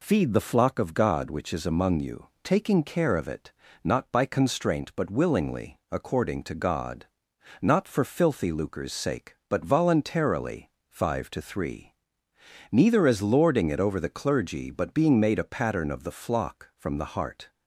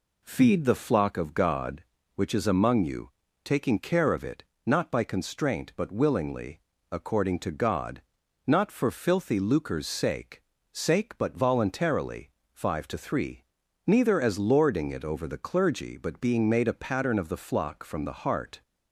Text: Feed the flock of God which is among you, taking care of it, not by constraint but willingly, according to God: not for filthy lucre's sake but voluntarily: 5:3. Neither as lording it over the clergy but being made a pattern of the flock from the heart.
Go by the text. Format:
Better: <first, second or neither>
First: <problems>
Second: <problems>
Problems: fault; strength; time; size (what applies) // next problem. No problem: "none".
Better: first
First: none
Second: says "sake" twice; at 10.7 s